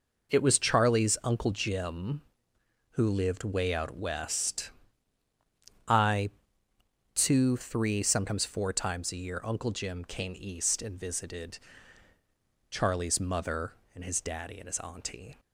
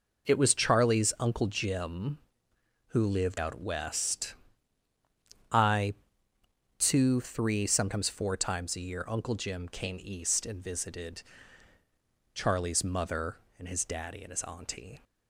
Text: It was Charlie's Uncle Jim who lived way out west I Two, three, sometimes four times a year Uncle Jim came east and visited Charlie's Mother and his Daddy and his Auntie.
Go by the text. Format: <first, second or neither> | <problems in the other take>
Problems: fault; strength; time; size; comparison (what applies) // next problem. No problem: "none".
first | skips "way"; at 3.3 s // pauses between "west" and "I"; at 4.3 s; 1.1 s long; also in the first // pauses between "I" and "Two"; noticeable; at 5.9 s; 0.86 s long; noticeable in the first // pauses between "visited" and "Charlie's"; at 11.2 s; 1.1 s long; also in the first